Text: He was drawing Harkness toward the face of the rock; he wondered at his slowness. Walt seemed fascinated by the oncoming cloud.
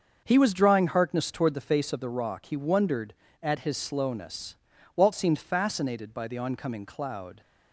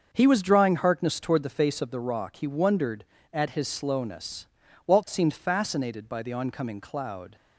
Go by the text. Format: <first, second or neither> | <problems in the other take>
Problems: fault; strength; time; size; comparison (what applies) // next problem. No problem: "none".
neither | starts louder than the rest; the same in both